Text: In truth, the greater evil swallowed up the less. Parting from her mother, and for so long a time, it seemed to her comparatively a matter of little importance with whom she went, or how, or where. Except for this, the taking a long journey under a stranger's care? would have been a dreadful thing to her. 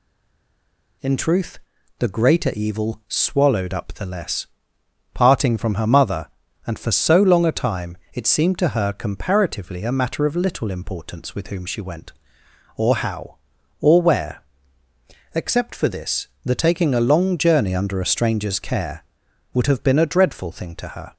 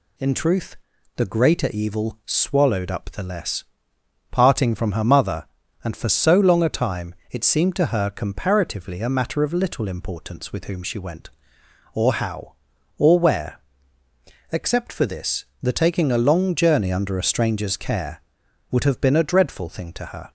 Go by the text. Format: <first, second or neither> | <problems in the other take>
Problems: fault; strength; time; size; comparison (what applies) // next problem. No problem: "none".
second | stays silent before the first word; until 1.0 s; 1.0 s long